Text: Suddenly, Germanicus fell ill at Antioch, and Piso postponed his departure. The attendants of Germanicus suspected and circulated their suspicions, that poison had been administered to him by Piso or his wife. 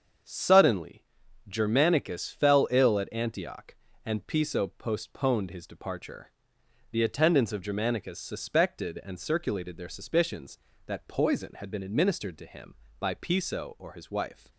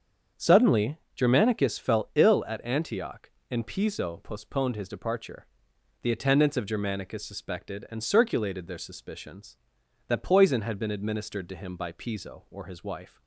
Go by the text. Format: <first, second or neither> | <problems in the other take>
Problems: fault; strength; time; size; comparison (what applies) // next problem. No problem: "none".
neither | starts louder than the rest; the same in both